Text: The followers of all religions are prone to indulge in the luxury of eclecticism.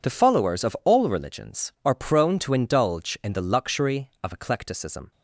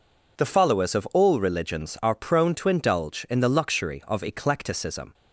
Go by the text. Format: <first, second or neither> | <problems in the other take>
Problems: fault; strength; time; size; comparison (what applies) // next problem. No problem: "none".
neither | none